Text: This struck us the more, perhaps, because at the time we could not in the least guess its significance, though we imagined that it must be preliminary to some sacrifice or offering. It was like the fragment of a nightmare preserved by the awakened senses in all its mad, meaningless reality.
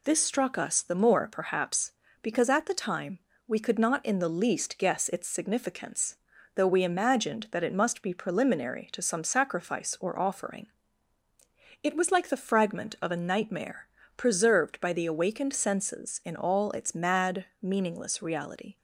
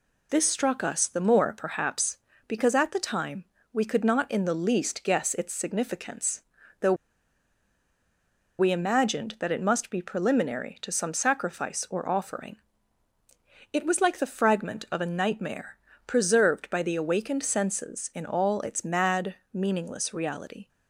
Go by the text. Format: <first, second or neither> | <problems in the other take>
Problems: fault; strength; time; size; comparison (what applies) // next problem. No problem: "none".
first | pauses between "time" and "we"; slight; at 3.4 s; 0.28 s long; slight in the first // pauses between "though" and "we"; strong; at 6.9 s; 1.6 s long // pauses between "nightmare" and "preserved"; slight; at 15.7 s; 0.30 s long; slight in the first